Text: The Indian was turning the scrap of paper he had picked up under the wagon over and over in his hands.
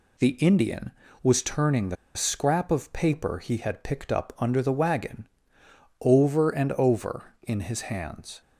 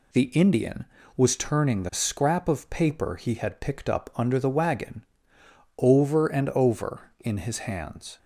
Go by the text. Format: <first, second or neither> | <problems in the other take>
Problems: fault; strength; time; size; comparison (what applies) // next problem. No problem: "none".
second | pauses between "the" and "scrap"; slight; at 1.9 s; 0.20 s long // pauses between "wagon" and "over"; noticeable; at 5.2 s; 0.72 s long; noticeable in the second